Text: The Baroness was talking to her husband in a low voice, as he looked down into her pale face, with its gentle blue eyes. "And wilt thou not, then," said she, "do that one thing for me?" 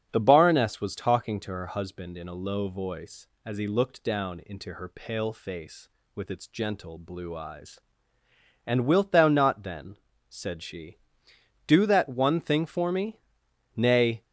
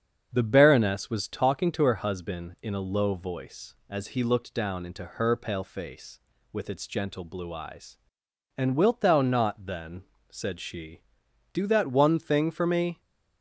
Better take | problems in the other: second | starts louder than the rest; strong; until 1.1 s; 7 dB; strong in the second // goes on to say "Nay"; slight; from 13.7 s on; 0.46 s long

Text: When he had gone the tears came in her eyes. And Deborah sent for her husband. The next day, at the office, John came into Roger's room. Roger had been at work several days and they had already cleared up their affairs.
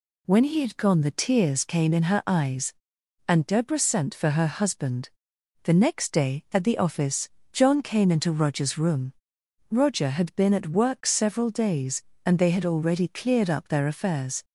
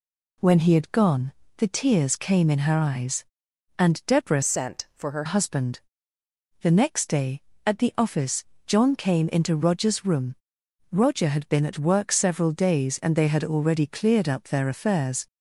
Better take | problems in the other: first | pauses between "gone" and "the"; slight; at 1.3 s; 0.24 s long // changes voice from "sent" to "her"; from 4.4 to 5.2 s; 0.8 s long

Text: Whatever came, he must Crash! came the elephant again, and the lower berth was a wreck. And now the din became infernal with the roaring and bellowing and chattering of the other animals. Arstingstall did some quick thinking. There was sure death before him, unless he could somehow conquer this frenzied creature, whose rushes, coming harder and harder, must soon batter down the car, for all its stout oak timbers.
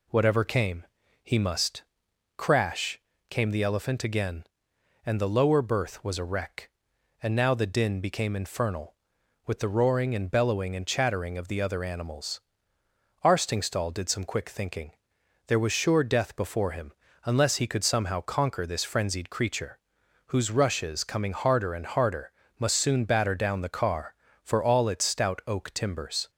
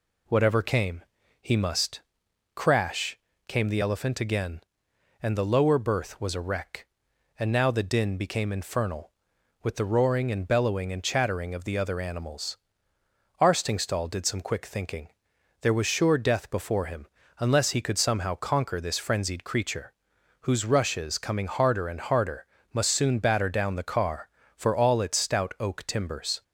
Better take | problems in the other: neither | pauses between "must" and "Crash"; noticeable; the same in both

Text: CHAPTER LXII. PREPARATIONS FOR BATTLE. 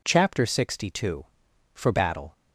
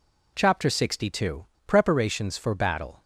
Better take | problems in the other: second | skips "PREPARATIONS"; at 1.5 s

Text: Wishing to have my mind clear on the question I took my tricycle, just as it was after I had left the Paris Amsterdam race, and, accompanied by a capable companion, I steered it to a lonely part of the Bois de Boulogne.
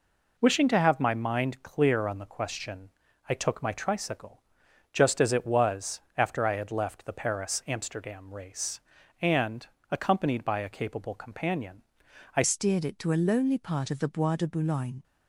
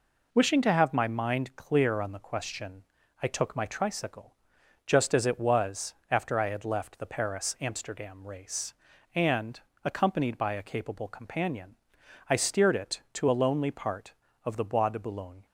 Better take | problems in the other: second | pauses between "question" and "I"; slight; at 2.9 s; 0.36 s long; slight in the second // pauses between "was" and "after"; slight; at 5.9 s; 0.16 s long; slight in the second // changes voice at "steered"; from 12.4 s on; 2.6 s long

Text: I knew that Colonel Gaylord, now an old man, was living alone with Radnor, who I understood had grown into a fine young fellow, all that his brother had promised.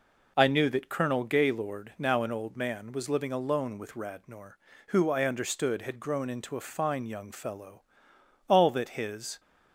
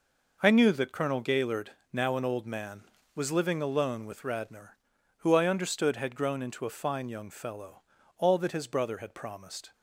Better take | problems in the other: second | stops before "brother had promised"; at 9.3 s

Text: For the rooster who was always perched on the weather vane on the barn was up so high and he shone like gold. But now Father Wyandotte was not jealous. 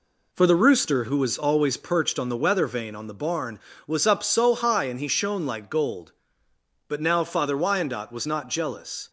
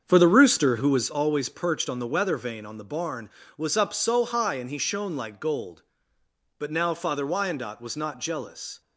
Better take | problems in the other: first | starts louder than the rest; strong; until 1.1 s; 7 dB

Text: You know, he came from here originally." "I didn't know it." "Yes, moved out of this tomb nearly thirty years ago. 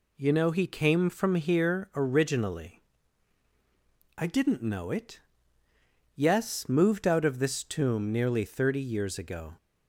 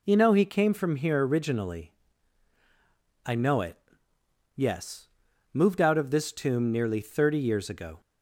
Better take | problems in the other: first | skips "didn't"; at 3.3 s

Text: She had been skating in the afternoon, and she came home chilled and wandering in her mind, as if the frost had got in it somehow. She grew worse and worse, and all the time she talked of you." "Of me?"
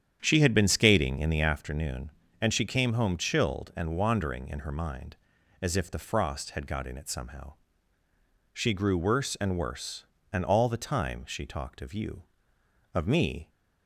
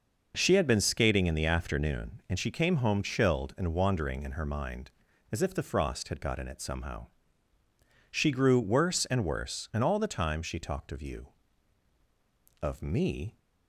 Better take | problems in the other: second | starts louder than the rest; strong; until 1.7 s; 9 dB

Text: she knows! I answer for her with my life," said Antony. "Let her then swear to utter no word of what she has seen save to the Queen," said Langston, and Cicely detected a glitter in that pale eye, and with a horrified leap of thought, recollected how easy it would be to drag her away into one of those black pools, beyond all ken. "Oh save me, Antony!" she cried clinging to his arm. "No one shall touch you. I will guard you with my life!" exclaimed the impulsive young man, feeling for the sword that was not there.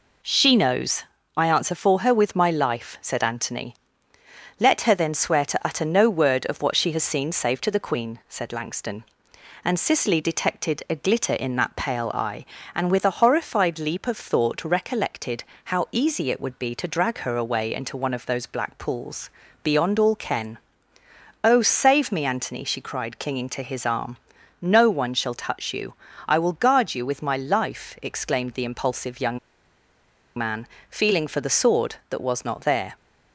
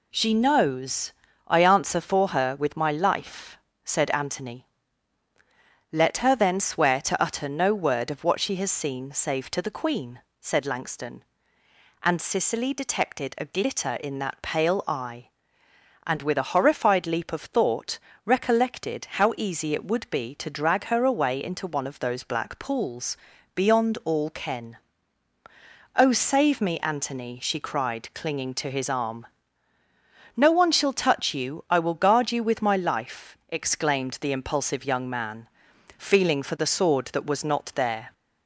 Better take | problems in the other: second | pauses between "recollected" and "how"; slight; at 15.4 s; 0.24 s long // pauses between "young" and "man"; at 29.3 s; 0.98 s long

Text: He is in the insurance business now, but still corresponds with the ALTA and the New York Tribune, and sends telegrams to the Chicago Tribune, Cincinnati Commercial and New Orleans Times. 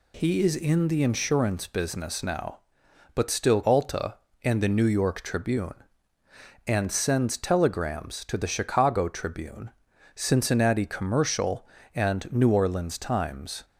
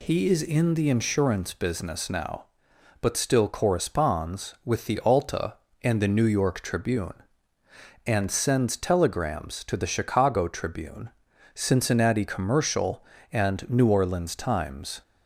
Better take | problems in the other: second | skips "corresponds with the"; at 3.6 s

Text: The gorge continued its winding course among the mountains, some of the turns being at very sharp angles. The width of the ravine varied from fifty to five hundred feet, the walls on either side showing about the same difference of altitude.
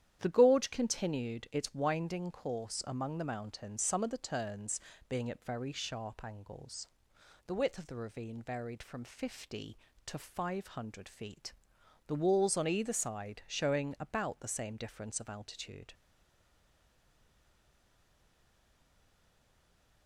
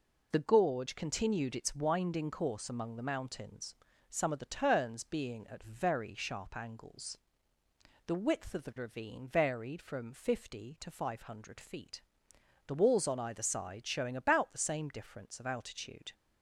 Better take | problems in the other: second | starts louder than the rest; strong; until 1.2 s; 10.5 dB // pauses between "turns" and "being"; slight; at 4.7 s; 0.30 s long // stays silent after the last word; strong; from 15.9 s on; 4.1 s long

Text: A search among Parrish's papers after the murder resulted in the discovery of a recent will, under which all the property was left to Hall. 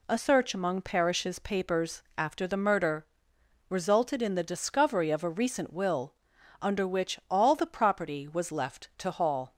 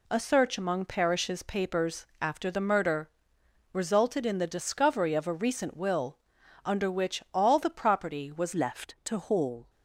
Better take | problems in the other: first | pauses between "papers" and "after"; slight; at 2.0 s; 0.16 s long; slight in the first // pauses between "murder" and "resulted"; noticeable; at 3.0 s; 0.64 s long; noticeable in the first // changes voice at "left"; from 8.5 s on; 1.1 s long

